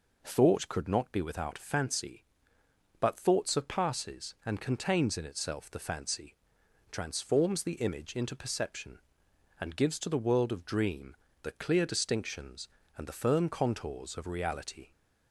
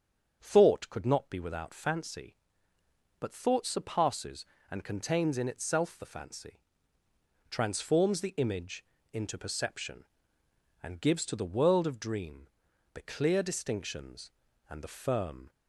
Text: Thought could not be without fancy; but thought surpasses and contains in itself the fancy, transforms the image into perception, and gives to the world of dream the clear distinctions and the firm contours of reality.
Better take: first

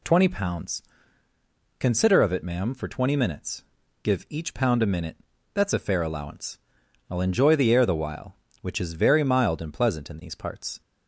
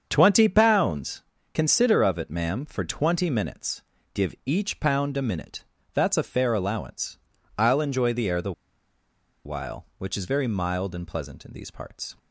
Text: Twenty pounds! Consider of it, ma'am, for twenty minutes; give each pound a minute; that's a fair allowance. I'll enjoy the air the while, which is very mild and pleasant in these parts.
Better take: first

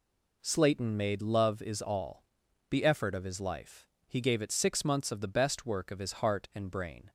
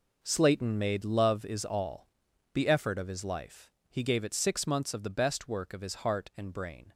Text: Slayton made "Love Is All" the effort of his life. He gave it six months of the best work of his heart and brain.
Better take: first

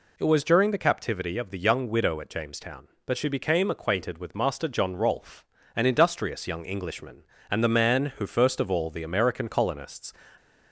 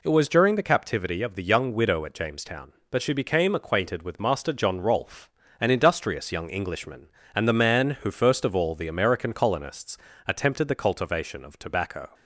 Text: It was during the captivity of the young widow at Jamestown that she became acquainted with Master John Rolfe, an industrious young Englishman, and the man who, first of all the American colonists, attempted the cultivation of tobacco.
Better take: second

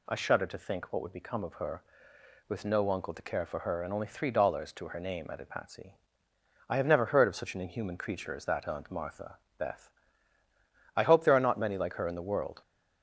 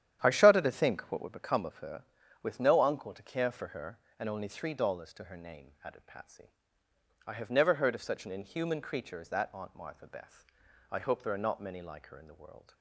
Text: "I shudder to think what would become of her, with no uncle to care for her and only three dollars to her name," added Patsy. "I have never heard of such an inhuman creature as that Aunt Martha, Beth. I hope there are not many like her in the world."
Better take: first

